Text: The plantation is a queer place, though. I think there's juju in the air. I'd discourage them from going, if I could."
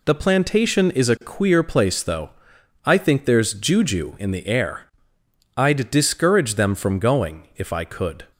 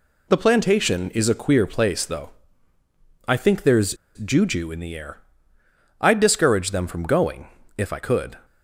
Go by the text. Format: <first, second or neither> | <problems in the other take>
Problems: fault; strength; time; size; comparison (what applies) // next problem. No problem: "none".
first | pauses between "there's" and "juju"; slight; at 3.9 s; 0.21 s long